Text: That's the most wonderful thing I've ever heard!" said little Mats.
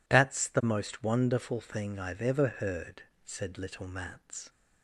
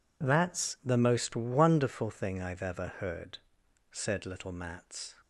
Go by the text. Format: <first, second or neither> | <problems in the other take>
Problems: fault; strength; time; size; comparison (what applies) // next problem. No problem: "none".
neither | none